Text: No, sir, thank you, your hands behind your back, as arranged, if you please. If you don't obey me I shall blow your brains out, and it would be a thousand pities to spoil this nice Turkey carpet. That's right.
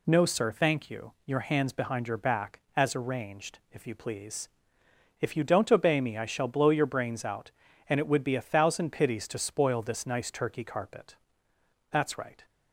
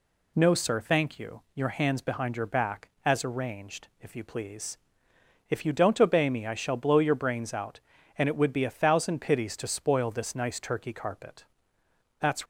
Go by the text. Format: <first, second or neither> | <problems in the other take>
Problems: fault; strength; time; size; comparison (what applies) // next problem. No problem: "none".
first | stops before "right"; at 12.4 s